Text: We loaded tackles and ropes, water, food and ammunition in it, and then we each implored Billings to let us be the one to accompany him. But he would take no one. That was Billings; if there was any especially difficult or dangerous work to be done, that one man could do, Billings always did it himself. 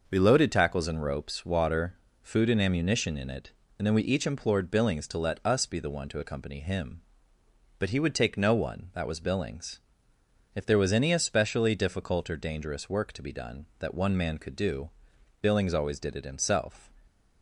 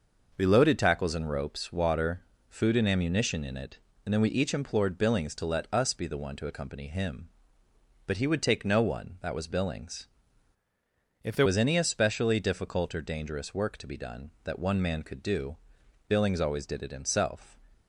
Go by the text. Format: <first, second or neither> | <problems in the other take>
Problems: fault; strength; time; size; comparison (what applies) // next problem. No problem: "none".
first | changes voice from "if" to "there"; from 11.2 to 11.4 s; 0.2 s long